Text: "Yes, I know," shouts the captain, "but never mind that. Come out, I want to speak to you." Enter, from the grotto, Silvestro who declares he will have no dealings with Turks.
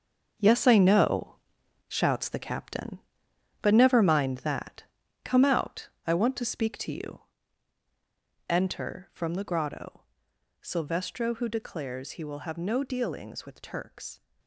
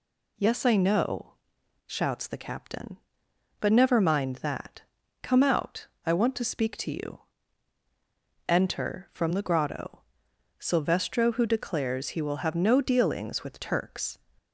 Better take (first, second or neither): second